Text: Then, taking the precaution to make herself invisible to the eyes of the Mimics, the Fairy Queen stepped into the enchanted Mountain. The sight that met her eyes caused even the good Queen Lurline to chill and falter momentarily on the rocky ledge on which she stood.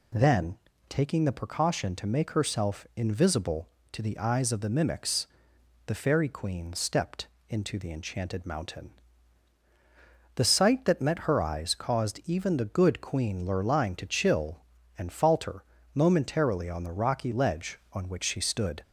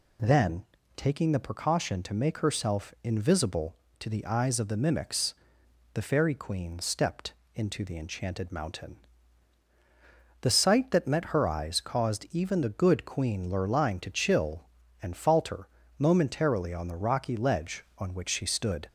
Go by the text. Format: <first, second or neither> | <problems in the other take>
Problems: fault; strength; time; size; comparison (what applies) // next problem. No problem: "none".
neither | pauses between "stepped" and "into"; slight; the same in both // pauses between "falter" and "momentarily"; slight; the same in both